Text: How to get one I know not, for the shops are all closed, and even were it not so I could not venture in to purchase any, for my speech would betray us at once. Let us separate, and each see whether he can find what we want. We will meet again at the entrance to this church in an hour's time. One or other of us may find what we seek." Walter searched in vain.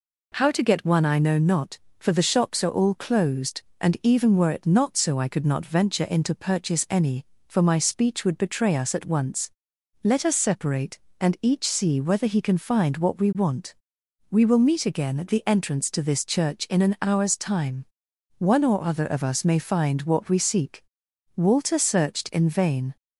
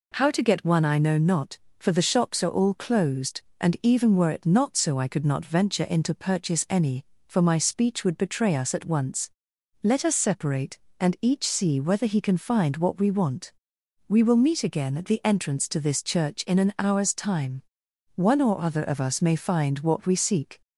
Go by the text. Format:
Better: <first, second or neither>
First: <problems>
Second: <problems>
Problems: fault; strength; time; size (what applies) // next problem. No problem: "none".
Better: first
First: none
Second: stops before "Walter searched in vain"; at 20.6 s